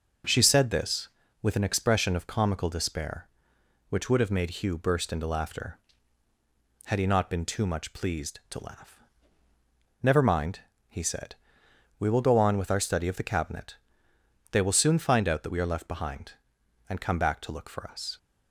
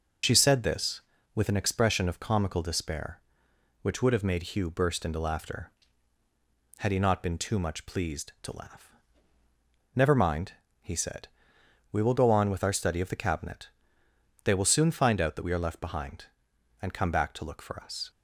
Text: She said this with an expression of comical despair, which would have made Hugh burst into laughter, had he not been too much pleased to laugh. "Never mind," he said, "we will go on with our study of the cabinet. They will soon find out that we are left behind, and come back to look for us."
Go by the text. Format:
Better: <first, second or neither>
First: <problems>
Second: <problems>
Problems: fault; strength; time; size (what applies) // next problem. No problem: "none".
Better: first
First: none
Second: loses the start of "She"; at 0.2 s; 65 ms